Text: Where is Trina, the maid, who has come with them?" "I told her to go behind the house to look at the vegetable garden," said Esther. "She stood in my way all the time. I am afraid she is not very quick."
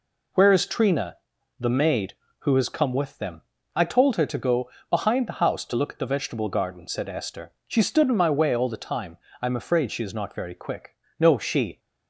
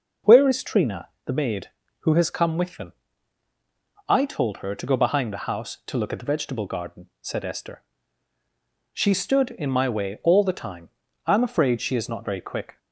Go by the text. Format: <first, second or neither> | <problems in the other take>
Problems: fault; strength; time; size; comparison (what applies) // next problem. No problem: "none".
second | pauses between "go" and "behind"; slight; at 4.6 s; 0.20 s long // goes on to say "No she"; from 11.1 s on; 0.60 s long